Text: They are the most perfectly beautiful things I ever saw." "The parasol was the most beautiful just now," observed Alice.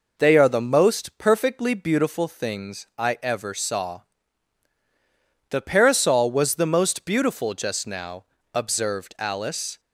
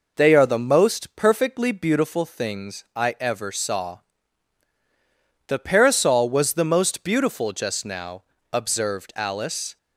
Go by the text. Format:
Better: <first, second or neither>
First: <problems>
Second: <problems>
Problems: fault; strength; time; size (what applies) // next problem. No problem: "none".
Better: neither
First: none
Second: none